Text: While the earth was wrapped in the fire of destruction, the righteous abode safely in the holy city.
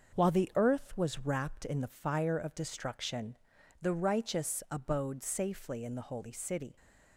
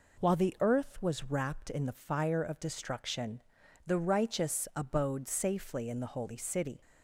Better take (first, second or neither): second